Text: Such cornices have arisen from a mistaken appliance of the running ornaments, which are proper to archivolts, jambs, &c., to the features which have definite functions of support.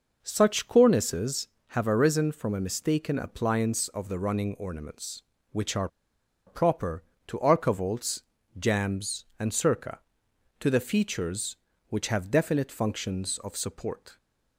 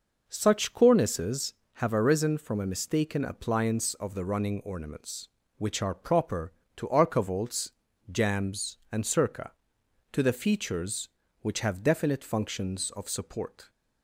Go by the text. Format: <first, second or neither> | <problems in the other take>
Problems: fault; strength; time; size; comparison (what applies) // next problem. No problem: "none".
second | pauses between "are" and "proper"; noticeable; at 5.8 s; 0.58 s long